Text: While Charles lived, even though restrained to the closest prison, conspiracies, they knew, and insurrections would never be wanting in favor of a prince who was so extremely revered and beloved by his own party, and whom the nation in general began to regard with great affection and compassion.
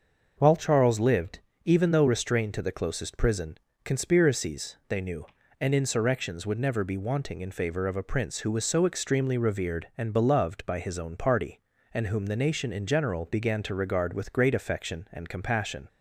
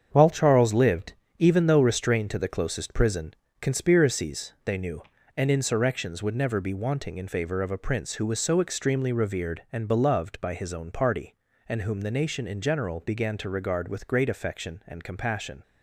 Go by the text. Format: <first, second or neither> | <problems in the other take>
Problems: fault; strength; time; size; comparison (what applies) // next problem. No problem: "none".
first | gets quieter; strong; throughout; 8.5 dB // starts louder than the rest; strong; until 1.1 s; 7.5 dB; also in the first